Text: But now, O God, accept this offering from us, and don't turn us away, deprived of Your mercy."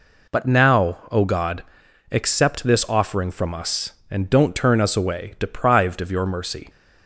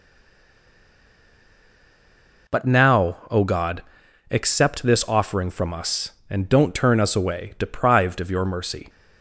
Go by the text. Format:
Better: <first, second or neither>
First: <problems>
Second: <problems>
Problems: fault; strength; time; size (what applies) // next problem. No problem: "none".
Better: first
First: none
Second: stays silent before the first word; until 2.4 s; 2.4 s long